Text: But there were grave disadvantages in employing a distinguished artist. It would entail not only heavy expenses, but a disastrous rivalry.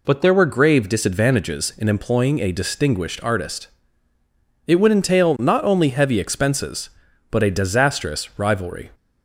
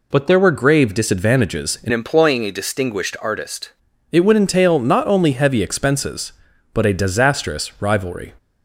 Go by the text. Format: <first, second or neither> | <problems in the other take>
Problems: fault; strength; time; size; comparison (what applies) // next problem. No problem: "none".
first | changes voice from "employing" to "artist"; from 1.9 to 3.7 s; 1.8 s long